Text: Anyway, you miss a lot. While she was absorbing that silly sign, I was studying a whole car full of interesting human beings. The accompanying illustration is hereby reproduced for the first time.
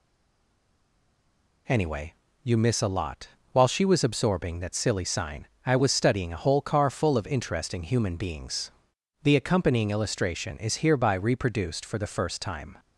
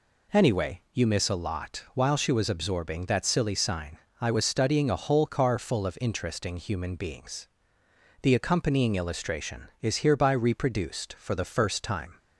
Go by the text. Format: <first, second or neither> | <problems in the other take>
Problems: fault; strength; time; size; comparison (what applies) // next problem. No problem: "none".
second | stays silent before the first word; noticeable; until 1.6 s; 1.6 s long